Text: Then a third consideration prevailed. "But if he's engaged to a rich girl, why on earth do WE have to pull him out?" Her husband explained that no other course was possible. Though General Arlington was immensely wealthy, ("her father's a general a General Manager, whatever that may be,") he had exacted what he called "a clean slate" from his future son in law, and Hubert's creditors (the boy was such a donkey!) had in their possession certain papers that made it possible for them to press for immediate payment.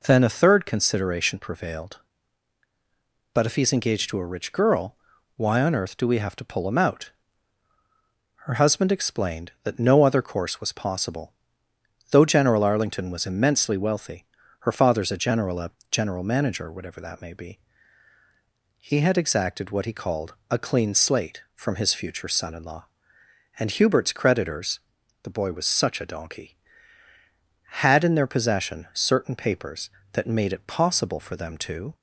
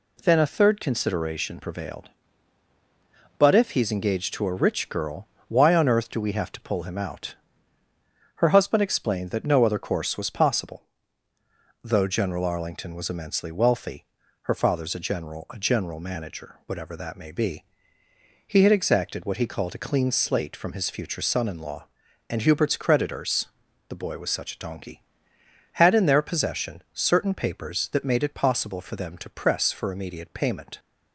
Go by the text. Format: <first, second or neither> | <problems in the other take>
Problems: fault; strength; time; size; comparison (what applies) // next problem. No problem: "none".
second | pauses between "a" and "General"; slight; at 15.7 s; 0.20 s long // pauses between "called" and "a"; slight; at 20.3 s; 0.16 s long // stops before "press for immediate payment"; at 31.9 s